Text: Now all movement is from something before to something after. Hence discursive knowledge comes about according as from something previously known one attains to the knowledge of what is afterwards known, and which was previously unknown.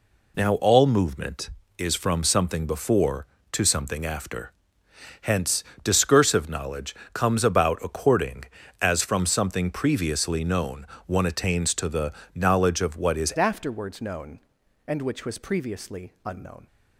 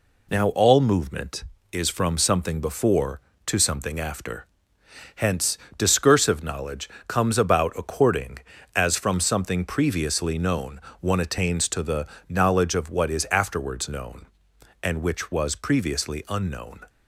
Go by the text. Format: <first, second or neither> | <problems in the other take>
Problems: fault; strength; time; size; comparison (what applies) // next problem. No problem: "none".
second | pauses between "Hence" and "discursive"; slight; at 5.6 s; 0.18 s long; slight in the second // pauses between "knowledge" and "comes"; slight; at 6.9 s; 0.20 s long; slight in the second // pauses between "known" and "one"; slight; at 10.8 s; 0.20 s long; slight in the second // pauses between "the" and "knowledge"; slight; at 12.1 s; 0.22 s long; slight in the second // changes voice at "afterwards"; from 13.3 s on; 3.3 s long